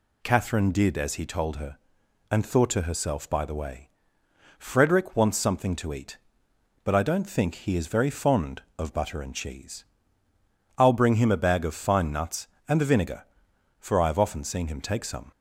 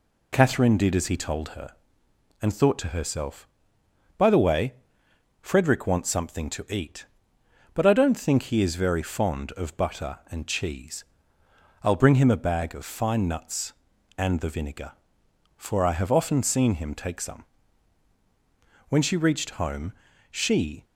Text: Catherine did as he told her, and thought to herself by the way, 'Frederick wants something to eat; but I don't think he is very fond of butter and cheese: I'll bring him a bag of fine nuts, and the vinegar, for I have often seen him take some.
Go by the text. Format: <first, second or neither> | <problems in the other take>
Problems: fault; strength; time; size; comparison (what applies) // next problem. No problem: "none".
first | goes on to say "When she reached home she"; strong; from 18.8 s on; 1.9 s long